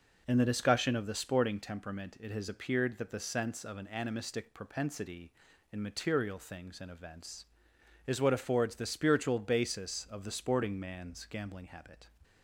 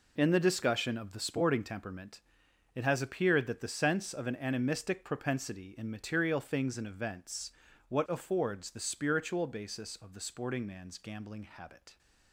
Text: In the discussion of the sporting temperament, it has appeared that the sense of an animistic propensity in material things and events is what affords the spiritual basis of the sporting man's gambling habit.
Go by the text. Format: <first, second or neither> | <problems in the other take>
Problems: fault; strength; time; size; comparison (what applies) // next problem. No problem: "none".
first | skips "is"; at 7.6 s